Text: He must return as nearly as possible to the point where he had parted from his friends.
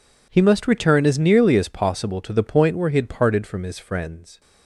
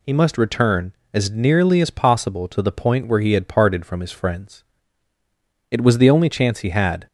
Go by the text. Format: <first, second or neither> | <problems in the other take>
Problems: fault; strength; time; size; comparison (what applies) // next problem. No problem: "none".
first | goes on to say "It was the only chance he had"; from 5.7 s on; 1.3 s long